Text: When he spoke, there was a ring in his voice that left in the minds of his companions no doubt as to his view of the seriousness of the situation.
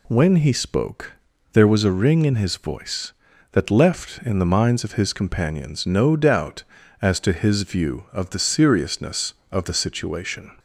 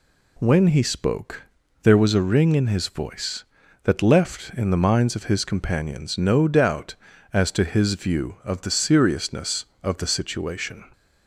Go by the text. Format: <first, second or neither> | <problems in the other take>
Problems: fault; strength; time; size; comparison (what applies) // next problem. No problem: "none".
neither | none